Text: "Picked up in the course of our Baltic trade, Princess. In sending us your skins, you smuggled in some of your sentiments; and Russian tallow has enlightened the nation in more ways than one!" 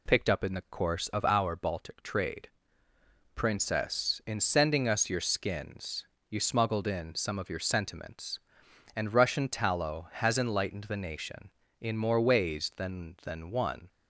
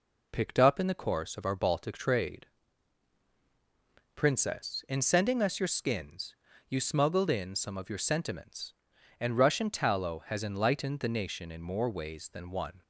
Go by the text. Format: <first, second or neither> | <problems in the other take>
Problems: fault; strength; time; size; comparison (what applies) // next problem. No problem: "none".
second | says "than" twice; at 13.2 s